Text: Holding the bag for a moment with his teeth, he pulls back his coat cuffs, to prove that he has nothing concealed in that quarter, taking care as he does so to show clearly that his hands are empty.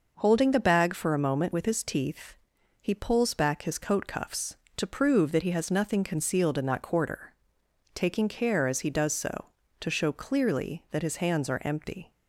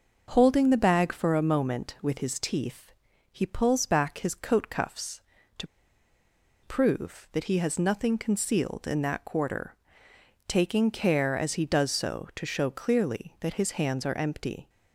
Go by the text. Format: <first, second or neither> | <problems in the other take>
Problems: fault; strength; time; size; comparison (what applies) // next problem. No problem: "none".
first | starts louder than the rest; until 1.3 s; 6 dB // pauses between "to" and "prove"; noticeable; at 5.6 s; 0.97 s long